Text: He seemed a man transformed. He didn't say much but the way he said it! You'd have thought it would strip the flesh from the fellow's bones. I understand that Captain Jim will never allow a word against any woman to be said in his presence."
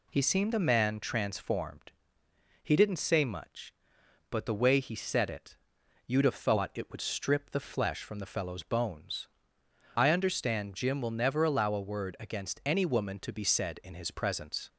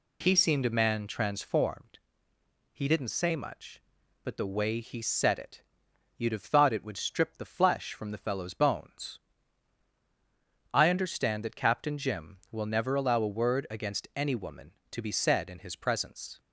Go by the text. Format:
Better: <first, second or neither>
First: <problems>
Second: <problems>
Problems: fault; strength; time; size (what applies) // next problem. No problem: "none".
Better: second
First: skips "that Captain"; at 10.7 s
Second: none